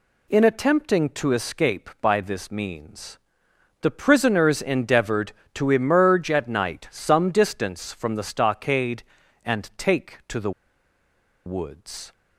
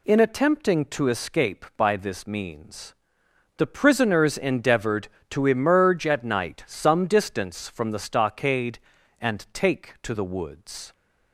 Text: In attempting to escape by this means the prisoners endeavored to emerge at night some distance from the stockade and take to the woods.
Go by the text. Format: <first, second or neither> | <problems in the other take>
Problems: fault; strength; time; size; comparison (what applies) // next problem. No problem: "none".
second | pauses between "means" and "the"; noticeable; at 3.1 s; 0.64 s long; noticeable in the second // pauses between "the" and "woods"; noticeable; at 10.5 s; 0.95 s long